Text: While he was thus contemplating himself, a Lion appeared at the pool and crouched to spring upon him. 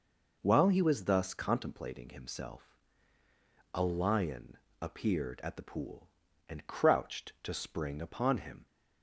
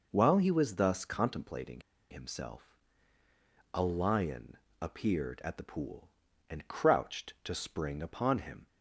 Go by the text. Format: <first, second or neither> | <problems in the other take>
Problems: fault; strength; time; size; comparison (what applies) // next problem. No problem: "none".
first | pauses between "contemplating" and "himself"; slight; at 1.8 s; 0.30 s long // pauses between "Lion" and "appeared"; slight; at 4.5 s; 0.22 s long; slight in the first